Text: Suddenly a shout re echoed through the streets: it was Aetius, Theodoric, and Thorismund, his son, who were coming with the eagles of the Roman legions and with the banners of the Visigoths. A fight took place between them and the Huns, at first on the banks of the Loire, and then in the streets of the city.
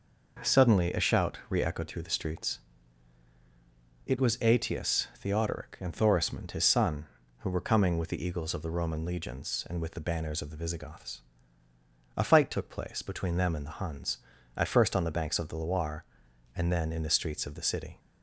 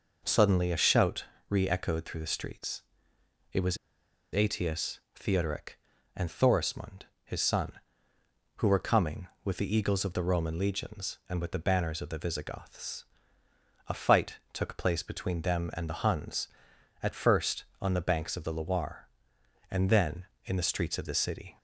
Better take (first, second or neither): first